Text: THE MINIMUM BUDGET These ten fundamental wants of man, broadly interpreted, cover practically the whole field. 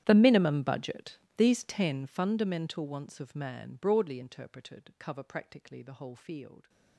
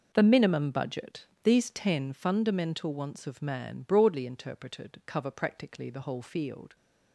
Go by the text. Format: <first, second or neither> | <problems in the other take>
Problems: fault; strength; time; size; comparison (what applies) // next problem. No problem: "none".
second | gets quieter; strong; throughout; 23.5 dB // pauses between "BUDGET" and "These"; slight; at 1.1 s; 0.20 s long; slight in the second